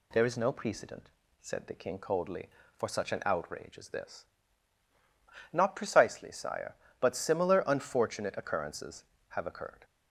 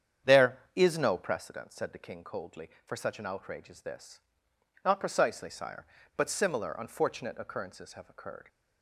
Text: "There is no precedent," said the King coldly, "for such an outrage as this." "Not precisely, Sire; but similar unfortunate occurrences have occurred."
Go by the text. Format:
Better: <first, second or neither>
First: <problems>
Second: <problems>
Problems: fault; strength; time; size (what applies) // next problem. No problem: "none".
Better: first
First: none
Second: starts louder than the rest; strong; until 1.5 s; 8.5 dB